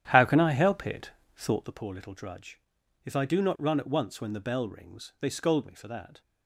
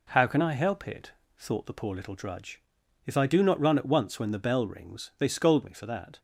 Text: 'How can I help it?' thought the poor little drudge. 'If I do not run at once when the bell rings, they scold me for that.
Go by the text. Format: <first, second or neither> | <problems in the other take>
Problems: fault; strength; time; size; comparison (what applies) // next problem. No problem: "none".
second | starts louder than the rest; strong; until 1.8 s; 10.5 dB